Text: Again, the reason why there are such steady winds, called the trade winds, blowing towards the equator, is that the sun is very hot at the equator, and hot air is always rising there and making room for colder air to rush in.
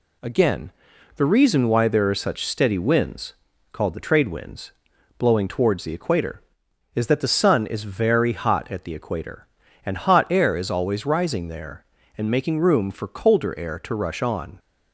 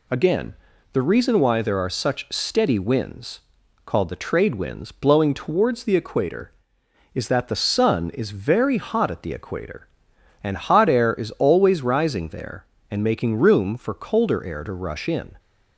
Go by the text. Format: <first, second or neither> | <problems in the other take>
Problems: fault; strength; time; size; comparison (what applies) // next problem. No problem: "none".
second | says "on" for "in"; at 14.2 s